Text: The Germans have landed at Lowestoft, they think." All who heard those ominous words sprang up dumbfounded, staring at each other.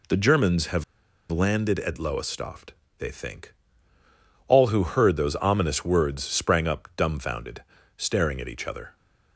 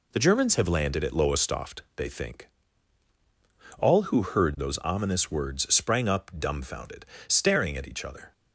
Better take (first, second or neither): second